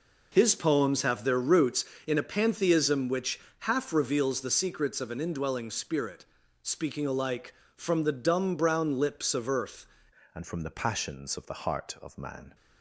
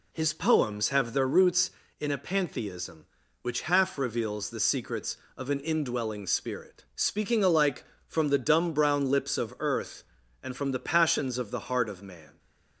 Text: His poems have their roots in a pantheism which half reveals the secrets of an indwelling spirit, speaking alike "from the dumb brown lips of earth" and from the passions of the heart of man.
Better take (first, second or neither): second